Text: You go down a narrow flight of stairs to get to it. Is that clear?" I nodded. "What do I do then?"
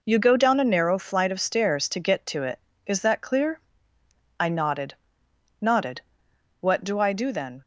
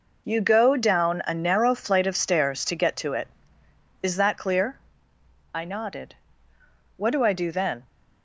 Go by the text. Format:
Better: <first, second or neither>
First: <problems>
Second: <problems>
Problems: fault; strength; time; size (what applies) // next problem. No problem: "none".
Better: second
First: says "nodded" twice; at 5.5 s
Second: none